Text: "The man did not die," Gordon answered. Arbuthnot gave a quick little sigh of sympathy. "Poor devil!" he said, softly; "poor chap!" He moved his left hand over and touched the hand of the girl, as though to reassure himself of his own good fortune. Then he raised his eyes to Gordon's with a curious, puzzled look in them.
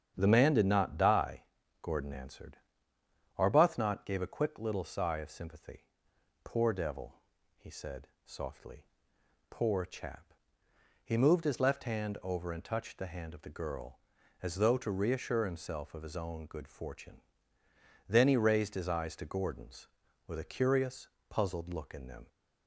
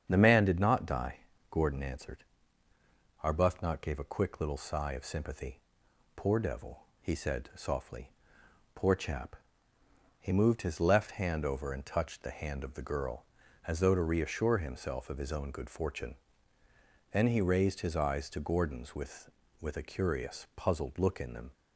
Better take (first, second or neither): first